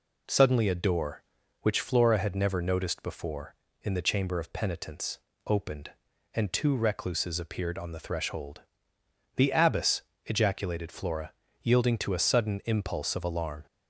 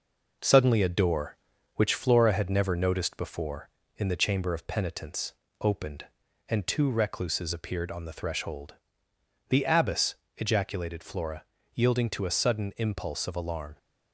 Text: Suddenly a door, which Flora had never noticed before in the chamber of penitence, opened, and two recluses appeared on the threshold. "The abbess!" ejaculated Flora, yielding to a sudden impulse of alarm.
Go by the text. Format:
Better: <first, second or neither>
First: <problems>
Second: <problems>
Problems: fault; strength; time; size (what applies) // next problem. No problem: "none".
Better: first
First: none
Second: gets quieter; slight; throughout; 3.5 dB